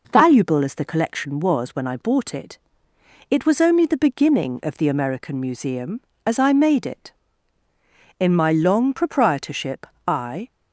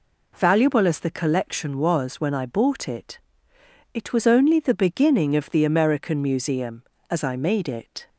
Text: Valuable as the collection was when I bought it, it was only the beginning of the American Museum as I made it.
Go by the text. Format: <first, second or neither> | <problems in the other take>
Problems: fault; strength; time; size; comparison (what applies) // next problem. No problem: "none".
second | goes on to say "In my long proprietorship I"; strong; from 8.1 s on; 2.2 s long